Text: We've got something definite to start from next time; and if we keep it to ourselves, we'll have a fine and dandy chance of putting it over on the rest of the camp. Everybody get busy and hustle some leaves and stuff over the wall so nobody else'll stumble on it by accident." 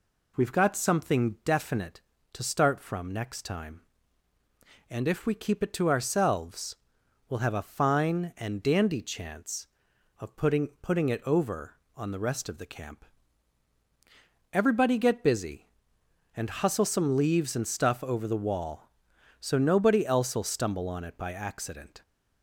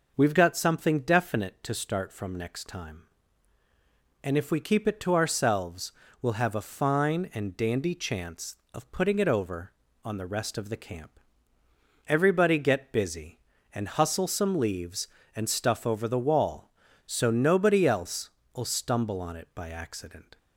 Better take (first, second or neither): second